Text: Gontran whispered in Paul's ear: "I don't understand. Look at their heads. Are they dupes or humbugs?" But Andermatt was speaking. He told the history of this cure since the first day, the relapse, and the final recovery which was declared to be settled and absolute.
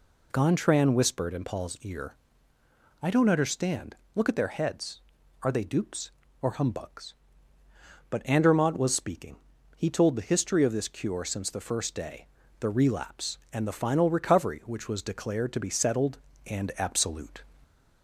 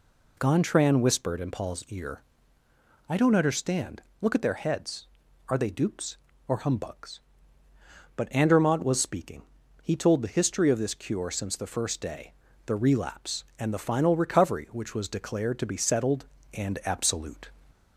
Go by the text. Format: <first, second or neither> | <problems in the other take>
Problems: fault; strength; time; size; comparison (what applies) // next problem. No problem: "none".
neither | none